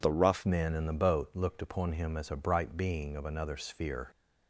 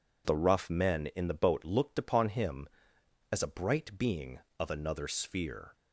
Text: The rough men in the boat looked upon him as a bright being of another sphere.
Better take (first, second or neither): second